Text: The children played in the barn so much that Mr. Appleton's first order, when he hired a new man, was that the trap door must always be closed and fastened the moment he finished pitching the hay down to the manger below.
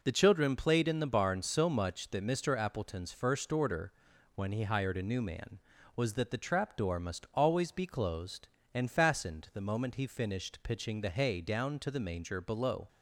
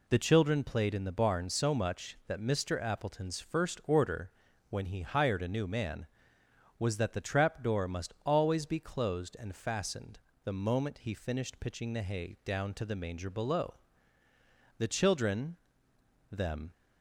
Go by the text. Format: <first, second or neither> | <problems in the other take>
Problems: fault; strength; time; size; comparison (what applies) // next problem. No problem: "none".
first | pauses between "fastened" and "the"; slight; at 10.2 s; 0.24 s long // goes on to say "The children them"; strong; from 14.7 s on; 1.9 s long